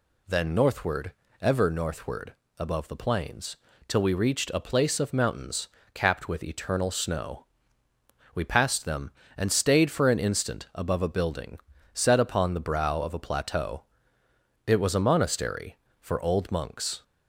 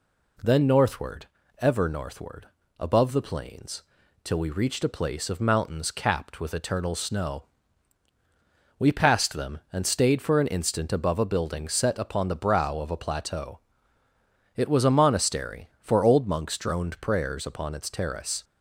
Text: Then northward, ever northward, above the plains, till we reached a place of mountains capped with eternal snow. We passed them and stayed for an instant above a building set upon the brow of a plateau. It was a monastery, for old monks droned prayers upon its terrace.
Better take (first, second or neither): second